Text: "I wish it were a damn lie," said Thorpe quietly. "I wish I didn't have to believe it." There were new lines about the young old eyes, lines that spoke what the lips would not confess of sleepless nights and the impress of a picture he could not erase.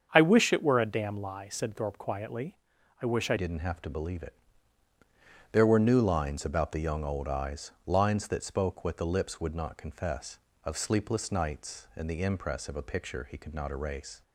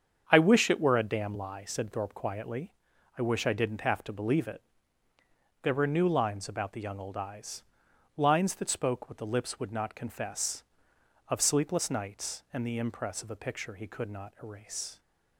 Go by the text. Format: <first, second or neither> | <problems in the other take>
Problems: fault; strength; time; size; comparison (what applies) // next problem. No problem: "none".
second | starts louder than the rest; strong; until 1.1 s; 7 dB; strong in the second // changes voice at "didn't"; from 3.3 s on; 10.9 s long